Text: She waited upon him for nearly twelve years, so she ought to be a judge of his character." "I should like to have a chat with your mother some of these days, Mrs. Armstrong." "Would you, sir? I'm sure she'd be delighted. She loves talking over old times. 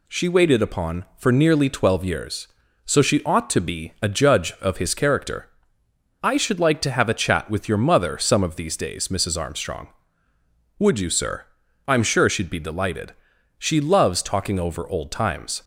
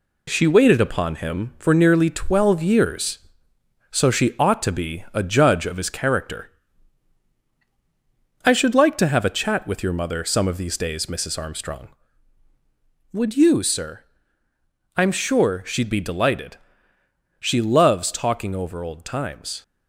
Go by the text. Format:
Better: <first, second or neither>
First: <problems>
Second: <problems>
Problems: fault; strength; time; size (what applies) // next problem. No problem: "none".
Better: second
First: skips "him"; at 1.1 s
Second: none